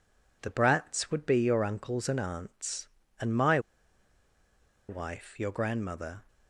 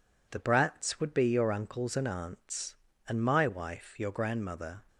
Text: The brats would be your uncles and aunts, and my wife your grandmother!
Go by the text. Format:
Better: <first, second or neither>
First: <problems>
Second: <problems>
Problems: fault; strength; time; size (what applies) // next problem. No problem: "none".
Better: second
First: pauses between "my" and "wife"; strong; at 3.5 s; 1.2 s long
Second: none